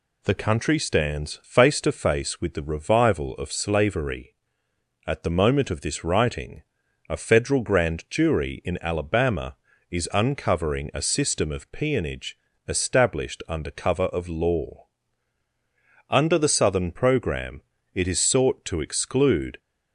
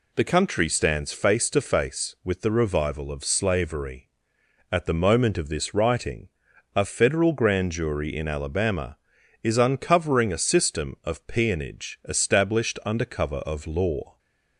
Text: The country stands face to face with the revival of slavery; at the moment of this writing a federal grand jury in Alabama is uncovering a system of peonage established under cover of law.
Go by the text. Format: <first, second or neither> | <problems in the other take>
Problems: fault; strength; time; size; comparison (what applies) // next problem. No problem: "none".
second | pauses between "writing" and "a"; noticeable; at 6.6 s; 0.46 s long; noticeable in the second // pauses between "peonage" and "established"; slight; at 12.3 s; 0.30 s long // goes on to say "Under the Southern program it is sought to exclude"; strong; from 16.0 s on; 3.5 s long